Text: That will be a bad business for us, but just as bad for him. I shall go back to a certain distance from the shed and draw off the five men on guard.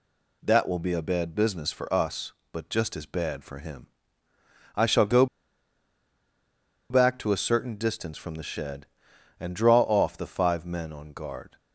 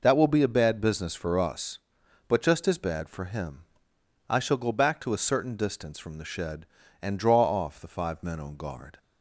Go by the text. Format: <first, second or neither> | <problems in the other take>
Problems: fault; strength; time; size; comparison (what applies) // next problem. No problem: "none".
second | pauses between "go" and "back"; strong; at 5.2 s; 1.6 s long